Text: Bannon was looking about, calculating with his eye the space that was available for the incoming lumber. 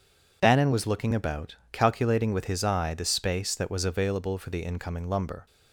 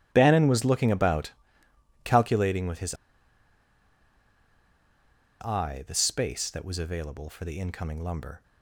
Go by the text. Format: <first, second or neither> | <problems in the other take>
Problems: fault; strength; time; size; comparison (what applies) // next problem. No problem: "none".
first | starts louder than the rest; strong; until 1.1 s; 14.5 dB // pauses between "his" and "eye"; strong; at 2.9 s; 2.4 s long